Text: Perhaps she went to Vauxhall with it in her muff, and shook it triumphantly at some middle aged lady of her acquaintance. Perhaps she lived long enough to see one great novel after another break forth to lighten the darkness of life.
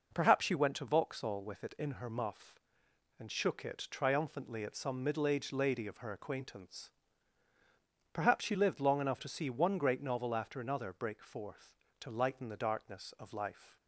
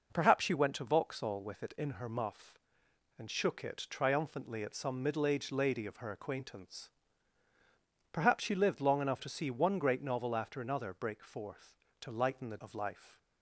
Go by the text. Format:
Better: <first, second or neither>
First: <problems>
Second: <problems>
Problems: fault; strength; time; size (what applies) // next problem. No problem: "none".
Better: first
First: none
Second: skips "darkness"; at 12.5 s